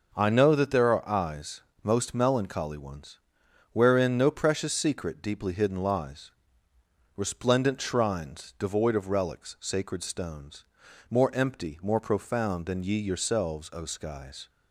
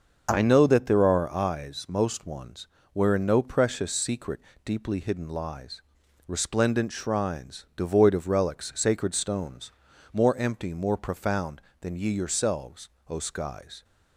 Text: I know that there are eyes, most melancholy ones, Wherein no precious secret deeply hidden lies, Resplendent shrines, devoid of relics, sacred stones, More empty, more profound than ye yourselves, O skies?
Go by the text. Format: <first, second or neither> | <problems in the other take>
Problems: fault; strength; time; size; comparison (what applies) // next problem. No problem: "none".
first | starts louder than the rest; noticeable; until 1.3 s; 6 dB // skips "melancholy"; at 2.2 s // pauses between "secret" and "deeply"; slight; at 4.3 s; 0.24 s long